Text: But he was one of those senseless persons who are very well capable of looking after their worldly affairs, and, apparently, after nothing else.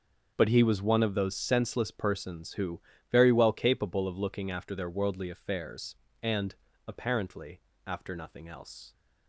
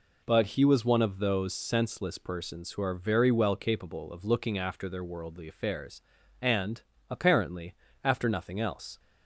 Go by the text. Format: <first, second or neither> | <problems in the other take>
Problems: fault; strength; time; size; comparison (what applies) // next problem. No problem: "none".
second | starts louder than the rest; until 1.3 s; 6.5 dB // skips "are"; at 2.9 s